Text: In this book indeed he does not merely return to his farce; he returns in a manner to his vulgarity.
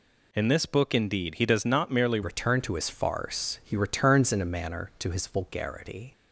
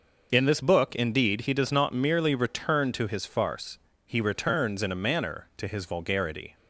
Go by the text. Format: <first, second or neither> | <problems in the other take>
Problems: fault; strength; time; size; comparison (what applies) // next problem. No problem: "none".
second | changes voice at "return"; from 2.2 s on; 3.9 s long